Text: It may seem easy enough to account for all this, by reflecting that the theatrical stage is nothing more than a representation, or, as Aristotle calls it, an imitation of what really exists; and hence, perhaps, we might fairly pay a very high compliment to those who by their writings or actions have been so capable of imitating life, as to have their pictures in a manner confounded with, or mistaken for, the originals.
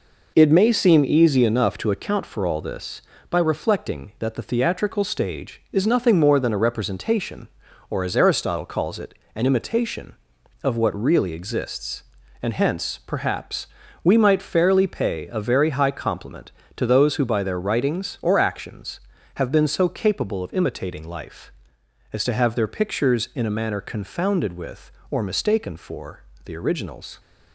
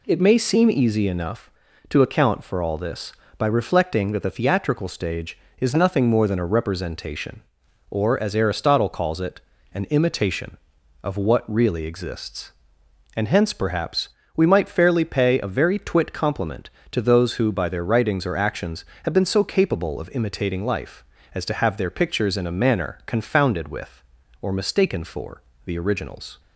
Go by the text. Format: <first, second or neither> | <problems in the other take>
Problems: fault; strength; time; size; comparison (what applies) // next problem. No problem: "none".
first | says "twit" for "high"; at 15.7 s